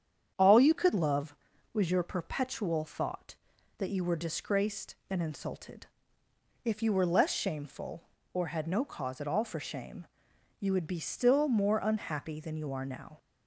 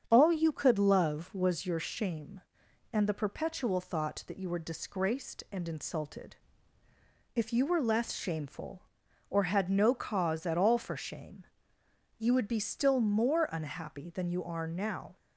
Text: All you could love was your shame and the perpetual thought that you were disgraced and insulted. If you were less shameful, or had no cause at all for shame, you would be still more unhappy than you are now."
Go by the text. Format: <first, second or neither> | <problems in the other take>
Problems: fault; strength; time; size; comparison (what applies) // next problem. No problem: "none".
second | starts louder than the rest; strong; until 1.3 s; 8.5 dB; strong in the second // skips "shame and the"; at 2.0 s